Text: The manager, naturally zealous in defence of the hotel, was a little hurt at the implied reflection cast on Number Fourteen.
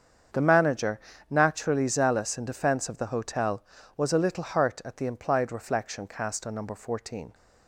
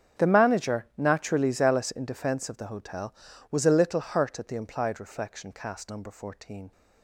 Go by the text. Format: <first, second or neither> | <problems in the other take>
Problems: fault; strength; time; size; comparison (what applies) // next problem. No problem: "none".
first | starts louder than the rest; strong; until 1.2 s; 7.5 dB; strong in the first // skips "on"; at 5.8 s